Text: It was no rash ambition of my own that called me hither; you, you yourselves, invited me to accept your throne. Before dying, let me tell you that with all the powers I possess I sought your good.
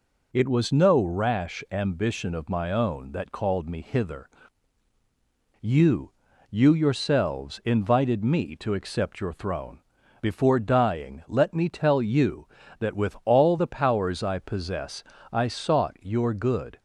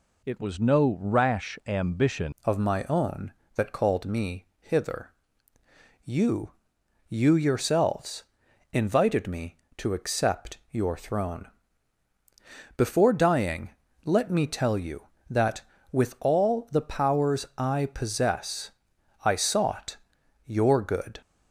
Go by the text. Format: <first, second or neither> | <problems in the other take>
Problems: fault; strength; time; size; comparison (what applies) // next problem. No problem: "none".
first | changes voice at "of"; from 2.4 s on; 18.7 s long // pauses between "possess" and "I"; noticeable; at 18.6 s; 0.54 s long; slight in the first // pauses between "sought" and "your"; noticeable; at 19.9 s; 0.50 s long